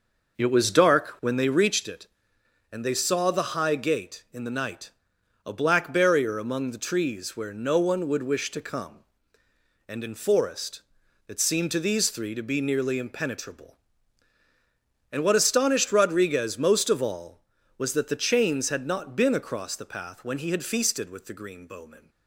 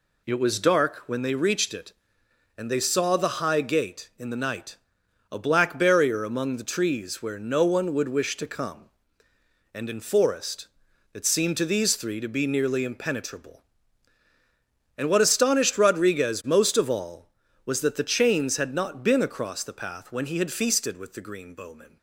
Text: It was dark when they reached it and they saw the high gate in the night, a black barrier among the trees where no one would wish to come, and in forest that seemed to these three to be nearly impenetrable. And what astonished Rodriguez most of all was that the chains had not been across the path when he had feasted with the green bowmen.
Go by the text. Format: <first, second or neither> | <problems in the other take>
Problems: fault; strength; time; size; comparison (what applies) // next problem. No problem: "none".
second | starts louder than the rest; noticeable; until 1.8 s; 5.5 dB